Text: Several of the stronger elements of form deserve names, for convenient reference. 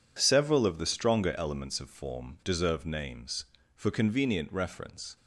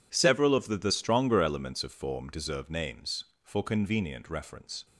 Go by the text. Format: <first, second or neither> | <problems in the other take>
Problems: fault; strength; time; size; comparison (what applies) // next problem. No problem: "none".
first | says "the" twice; at 0.7 s